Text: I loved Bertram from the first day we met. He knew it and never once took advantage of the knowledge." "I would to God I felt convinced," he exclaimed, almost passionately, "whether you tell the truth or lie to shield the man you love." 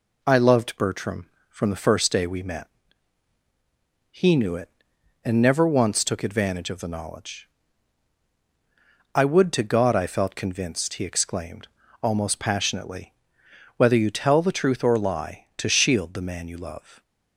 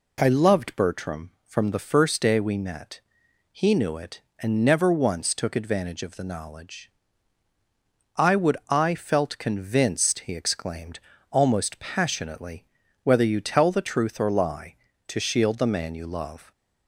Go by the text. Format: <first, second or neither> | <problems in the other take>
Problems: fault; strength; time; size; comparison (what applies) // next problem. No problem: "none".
first | skips "to God"; at 8.6 s